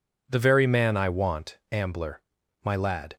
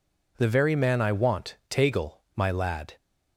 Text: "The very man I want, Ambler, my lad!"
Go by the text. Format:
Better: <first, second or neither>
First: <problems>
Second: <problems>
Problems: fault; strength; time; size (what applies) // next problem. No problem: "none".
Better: first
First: none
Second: says "Tagel" for "Ambler"; at 1.6 s